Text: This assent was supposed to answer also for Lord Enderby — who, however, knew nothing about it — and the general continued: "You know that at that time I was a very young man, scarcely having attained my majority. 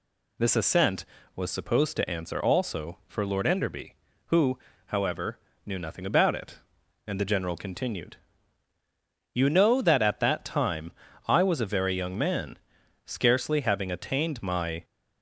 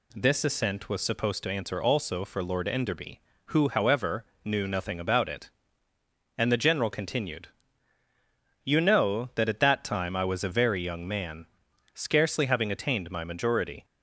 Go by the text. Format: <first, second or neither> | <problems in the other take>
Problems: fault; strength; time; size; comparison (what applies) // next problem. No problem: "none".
second | pauses between "time" and "I"; slight; at 10.9 s; 0.36 s long // stops before "majority"; at 14.8 s